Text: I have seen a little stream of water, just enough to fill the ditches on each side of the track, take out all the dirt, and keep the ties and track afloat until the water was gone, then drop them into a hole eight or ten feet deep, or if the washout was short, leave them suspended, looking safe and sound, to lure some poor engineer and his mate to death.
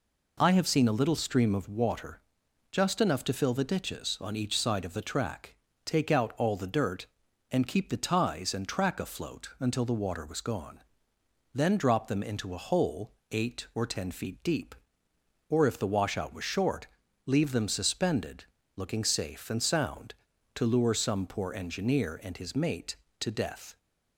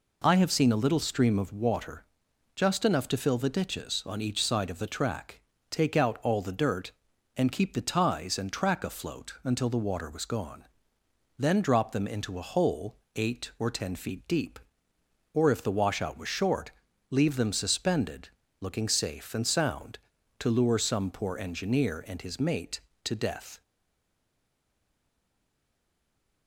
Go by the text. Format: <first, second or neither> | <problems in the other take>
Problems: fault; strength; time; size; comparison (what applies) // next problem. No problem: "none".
first | pauses between "hole" and "eight"; slight; at 12.9 s; 0.18 s long; slight in the first // stays silent after the last word; strong; from 23.6 s on; 2.8 s long